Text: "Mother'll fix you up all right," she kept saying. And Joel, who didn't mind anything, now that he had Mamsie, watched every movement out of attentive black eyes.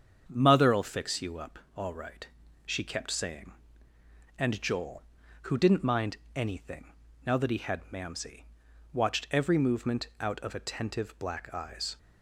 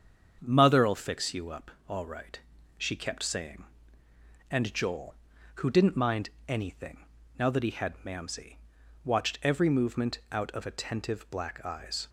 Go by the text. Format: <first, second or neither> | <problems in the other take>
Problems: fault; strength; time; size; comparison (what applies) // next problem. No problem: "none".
neither | starts louder than the rest; strong; the same in both // pauses between "up" and "all"; slight; the same in both // pauses between "mind" and "anything"; slight; the same in both